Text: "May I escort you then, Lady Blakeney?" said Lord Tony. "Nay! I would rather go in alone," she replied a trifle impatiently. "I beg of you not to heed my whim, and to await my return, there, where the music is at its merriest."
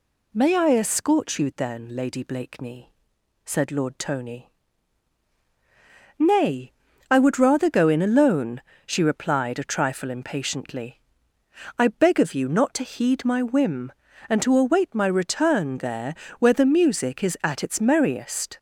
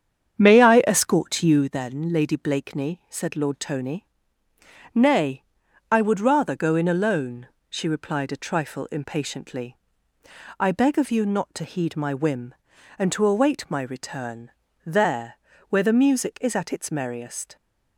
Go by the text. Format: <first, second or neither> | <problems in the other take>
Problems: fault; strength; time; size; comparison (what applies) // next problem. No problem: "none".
first | starts louder than the rest; strong; until 1.8 s; 8 dB